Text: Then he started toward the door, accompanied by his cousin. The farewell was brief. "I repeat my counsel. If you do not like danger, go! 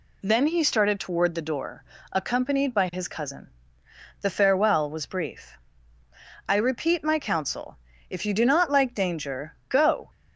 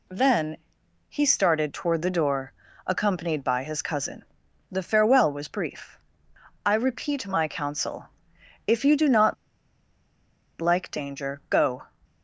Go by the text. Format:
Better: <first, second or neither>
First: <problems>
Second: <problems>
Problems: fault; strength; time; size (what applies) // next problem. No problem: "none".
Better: first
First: none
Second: pauses between "Then" and "he"; noticeable; at 0.5 s; 0.54 s long // pauses between "not" and "like"; at 9.3 s; 1.2 s long